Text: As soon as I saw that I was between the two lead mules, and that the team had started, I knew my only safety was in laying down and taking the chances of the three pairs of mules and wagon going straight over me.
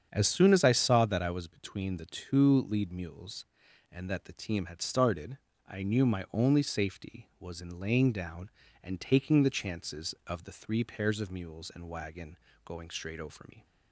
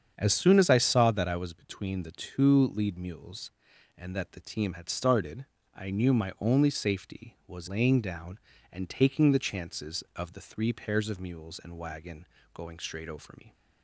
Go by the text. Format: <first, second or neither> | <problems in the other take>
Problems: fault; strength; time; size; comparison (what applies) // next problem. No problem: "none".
first | starts louder than the rest; strong; until 1.1 s; 7.5 dB; strong in the first // skips "in"; at 7.6 s // pauses between "wagon" and "going"; slight; at 12.2 s; 0.28 s long; slight in the first